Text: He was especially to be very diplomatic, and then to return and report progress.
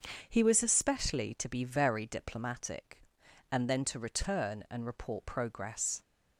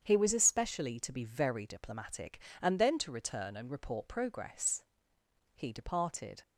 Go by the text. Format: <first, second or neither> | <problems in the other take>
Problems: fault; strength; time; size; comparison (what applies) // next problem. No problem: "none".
first | starts louder than the rest; strong; until 1.0 s; 8 dB; also in the first // goes on to say "He departed"; noticeable; from 5.5 s on; 0.88 s long